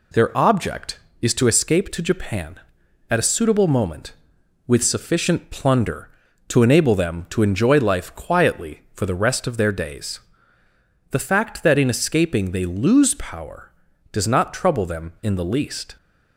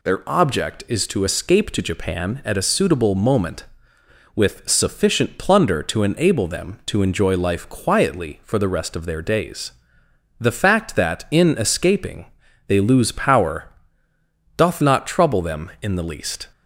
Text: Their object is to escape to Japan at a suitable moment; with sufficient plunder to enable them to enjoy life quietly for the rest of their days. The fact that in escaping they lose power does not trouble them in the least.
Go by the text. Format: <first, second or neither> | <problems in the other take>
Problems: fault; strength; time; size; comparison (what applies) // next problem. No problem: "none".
first | pauses between "escaping" and "they"; at 12.2 s; 0.40 s long // says "doth" for "does"; at 14.5 s